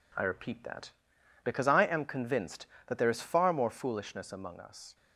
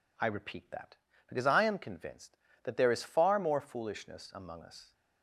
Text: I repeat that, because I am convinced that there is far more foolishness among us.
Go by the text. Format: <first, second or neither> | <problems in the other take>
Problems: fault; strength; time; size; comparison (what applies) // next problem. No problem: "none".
second | gets quieter; throughout; 3.5 dB